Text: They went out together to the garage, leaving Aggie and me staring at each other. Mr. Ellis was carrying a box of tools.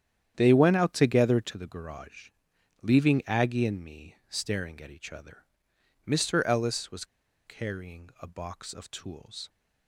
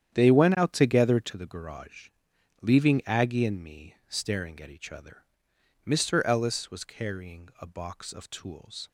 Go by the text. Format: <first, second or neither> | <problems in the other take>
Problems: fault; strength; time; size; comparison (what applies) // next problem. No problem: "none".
second | starts louder than the rest; strong; until 1.3 s; 9.5 dB; strong in the second // pauses between "was" and "carrying"; at 7.0 s; 0.41 s long